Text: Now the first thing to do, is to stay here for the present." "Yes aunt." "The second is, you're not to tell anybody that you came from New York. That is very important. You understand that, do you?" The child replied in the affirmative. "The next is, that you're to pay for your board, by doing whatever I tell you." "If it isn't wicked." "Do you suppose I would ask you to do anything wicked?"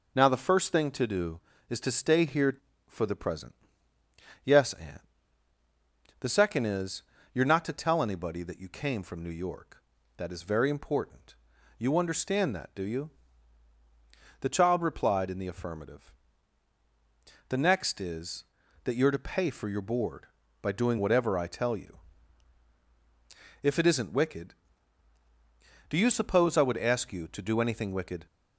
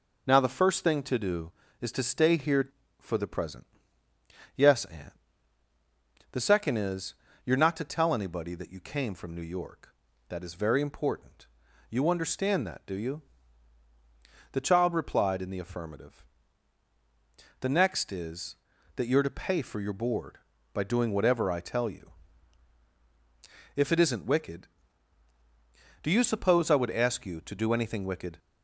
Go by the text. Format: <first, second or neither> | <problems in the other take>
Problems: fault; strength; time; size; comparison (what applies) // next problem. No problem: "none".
neither | none